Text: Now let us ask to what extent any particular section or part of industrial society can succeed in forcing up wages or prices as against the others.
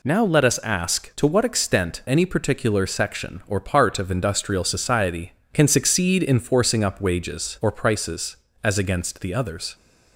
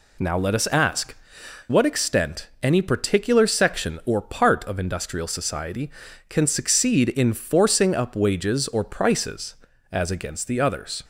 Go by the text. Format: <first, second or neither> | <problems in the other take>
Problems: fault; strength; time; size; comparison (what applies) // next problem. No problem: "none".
first | skips "to"; at 1.4 s